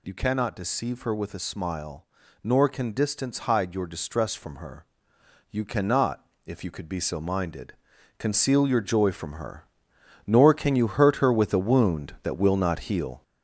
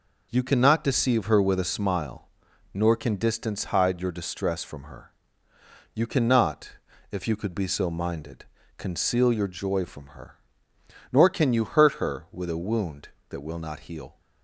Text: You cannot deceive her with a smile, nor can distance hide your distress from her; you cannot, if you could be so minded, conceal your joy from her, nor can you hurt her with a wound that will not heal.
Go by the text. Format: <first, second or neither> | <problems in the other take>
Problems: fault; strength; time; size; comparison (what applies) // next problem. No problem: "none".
second | gets louder; noticeable; throughout; 5.5 dB